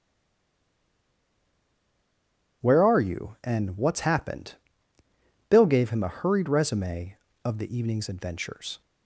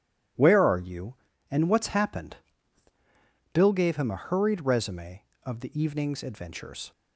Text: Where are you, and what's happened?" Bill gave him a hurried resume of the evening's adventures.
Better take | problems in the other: second | stays silent before the first word; strong; until 2.6 s; 2.6 s long

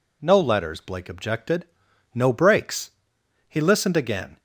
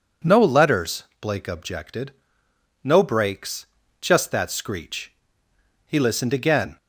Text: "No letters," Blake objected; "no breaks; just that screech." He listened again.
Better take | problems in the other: second | skips "just that screech"; at 3.1 s

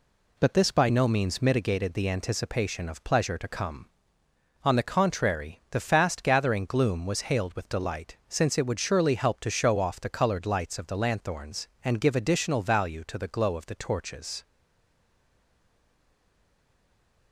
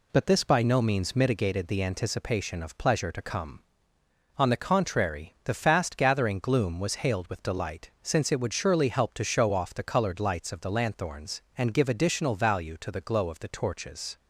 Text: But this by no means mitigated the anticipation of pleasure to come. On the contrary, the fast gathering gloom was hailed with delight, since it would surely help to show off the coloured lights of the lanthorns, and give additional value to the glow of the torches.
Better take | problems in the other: second | stays silent after the last word; strong; from 14.4 s on; 2.9 s long

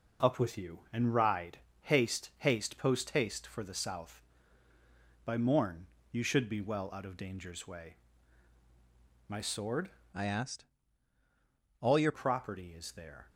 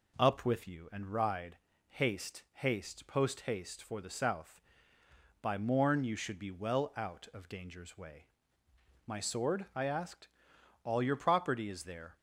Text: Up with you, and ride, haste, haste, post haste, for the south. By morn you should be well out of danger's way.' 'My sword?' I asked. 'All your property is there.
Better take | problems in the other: second | pauses between "morn" and "you"; slight; at 5.8 s; 0.24 s long // changes voice from "I" to "your"; from 10.1 to 12.1 s; 2.0 s long

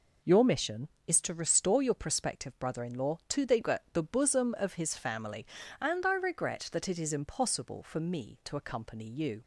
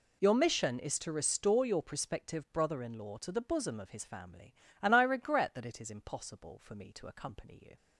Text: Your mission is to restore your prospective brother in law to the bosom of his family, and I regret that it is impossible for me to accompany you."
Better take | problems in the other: second | says "the" twice; at 3.9 s

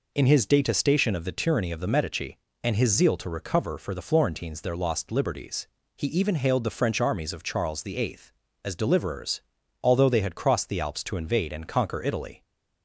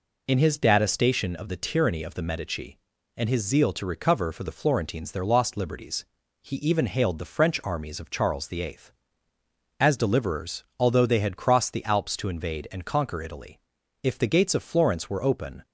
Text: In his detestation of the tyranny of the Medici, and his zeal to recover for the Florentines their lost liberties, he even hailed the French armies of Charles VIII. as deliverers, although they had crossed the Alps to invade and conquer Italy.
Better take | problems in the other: first | goes on to say "If the gates of Florence were open"; from 14.0 s on; 1.6 s long

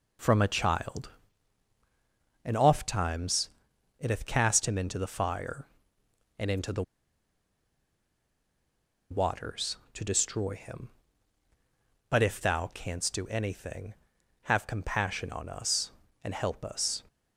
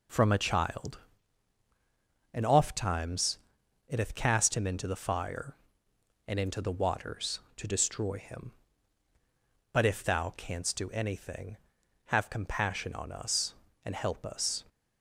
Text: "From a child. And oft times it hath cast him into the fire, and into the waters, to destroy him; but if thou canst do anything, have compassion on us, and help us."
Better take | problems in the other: second | pauses between "times" and "it"; noticeable; at 3.4 s; 0.50 s long; noticeable in the second // pauses between "the" and "waters"; strong; at 6.8 s; 2.2 s long

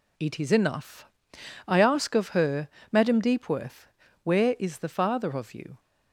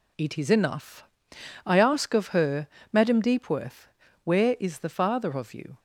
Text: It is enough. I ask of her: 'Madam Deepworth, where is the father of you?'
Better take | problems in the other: neither | none

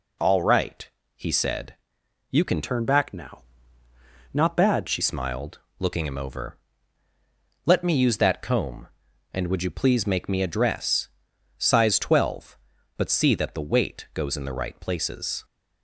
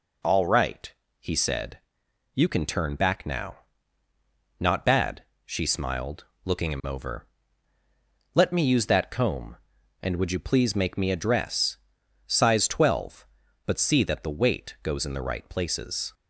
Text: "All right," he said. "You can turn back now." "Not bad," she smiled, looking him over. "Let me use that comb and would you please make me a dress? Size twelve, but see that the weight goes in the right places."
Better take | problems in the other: second | changes voice from "turn" to "she"; from 2.6 to 5.0 s; 2.4 s long

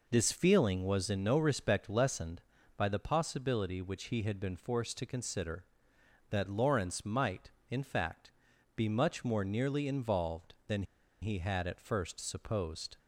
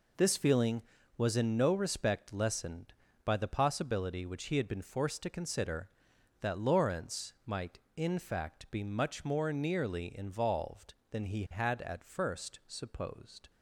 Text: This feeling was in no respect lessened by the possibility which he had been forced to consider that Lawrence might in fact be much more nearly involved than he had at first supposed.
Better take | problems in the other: second | pauses between "fact" and "be"; at 8.3 s; 0.44 s long // pauses between "than" and "he"; at 10.8 s; 0.38 s long

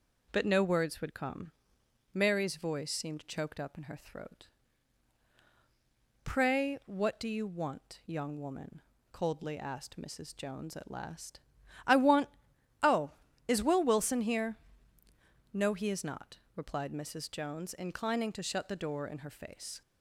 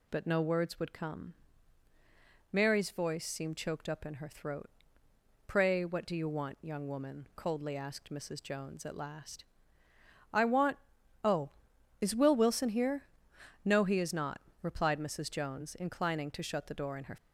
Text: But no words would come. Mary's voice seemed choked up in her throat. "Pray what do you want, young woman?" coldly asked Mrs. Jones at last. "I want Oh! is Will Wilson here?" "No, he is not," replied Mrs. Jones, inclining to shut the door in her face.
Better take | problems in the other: first | pauses between "want" and "Oh"; at 10.7 s; 0.44 s long; noticeable in the first // stops before "face"; at 17.1 s

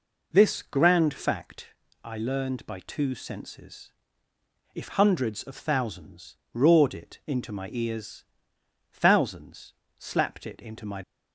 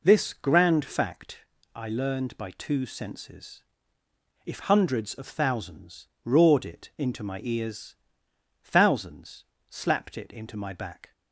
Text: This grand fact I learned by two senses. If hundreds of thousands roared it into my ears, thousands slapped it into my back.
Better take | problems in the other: second | pauses between "fact" and "I"; slight; at 1.7 s; 0.32 s long; slight in the second // pauses between "thousands" and "roared"; slight; at 6.3 s; 0.16 s long; slight in the second // pauses between "thousands" and "slapped"; slight; at 9.7 s; 0.26 s long; slight in the second // stops before "back"; at 11.0 s

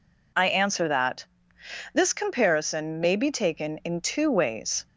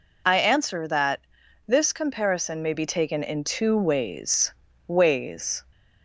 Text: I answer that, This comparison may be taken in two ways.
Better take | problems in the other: first | says "ways" twice; at 4.8 s

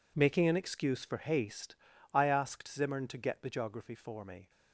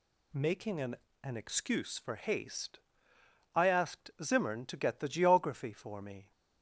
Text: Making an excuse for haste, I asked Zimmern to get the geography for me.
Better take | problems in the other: first | says "an" twice; at 1.2 s

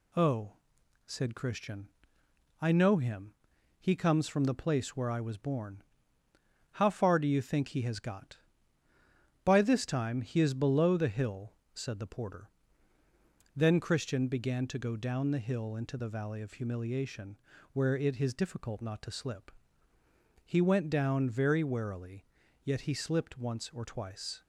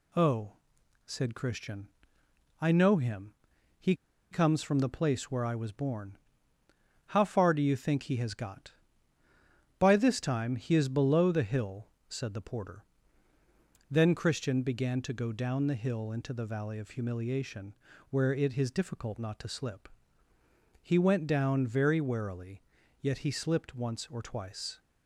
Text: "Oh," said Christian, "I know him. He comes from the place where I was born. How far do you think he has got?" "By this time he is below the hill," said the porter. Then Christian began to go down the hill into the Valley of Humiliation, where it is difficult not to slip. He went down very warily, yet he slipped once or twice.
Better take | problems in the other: first | pauses between "He" and "comes"; at 3.9 s; 0.36 s long

